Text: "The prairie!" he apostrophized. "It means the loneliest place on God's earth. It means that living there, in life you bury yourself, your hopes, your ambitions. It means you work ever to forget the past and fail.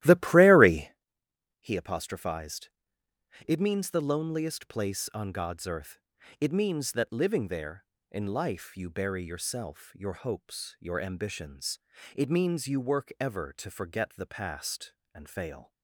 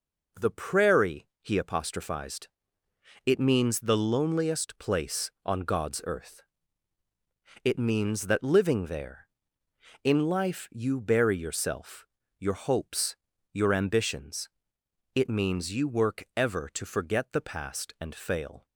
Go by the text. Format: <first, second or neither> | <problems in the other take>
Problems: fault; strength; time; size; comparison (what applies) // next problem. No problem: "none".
second | starts louder than the rest; strong; until 1.0 s; 14.5 dB